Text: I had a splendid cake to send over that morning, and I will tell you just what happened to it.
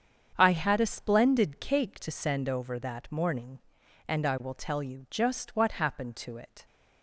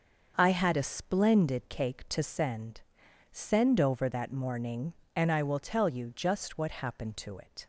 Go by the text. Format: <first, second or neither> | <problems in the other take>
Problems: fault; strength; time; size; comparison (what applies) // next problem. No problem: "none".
first | starts louder than the rest; until 1.3 s; 6.5 dB; strong in the first // says "send" twice; at 3.2 s